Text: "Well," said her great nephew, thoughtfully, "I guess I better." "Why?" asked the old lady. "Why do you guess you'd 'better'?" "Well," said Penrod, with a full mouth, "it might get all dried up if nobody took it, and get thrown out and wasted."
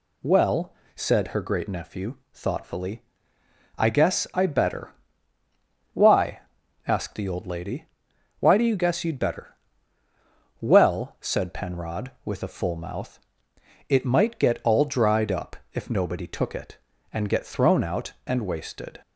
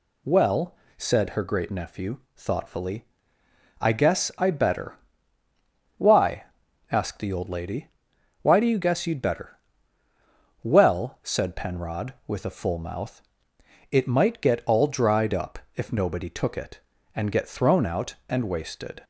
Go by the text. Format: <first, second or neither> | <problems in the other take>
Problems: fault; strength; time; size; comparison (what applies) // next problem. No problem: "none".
neither | pauses between "up" and "if"; slight; the same in both